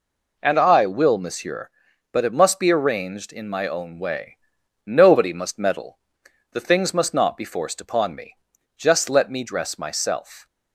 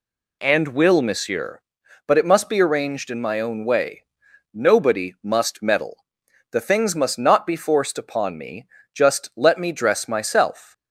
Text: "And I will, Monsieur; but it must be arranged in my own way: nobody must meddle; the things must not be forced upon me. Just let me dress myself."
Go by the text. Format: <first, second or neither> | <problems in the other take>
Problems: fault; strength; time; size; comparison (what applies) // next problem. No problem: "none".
first | skips "I"; at 0.6 s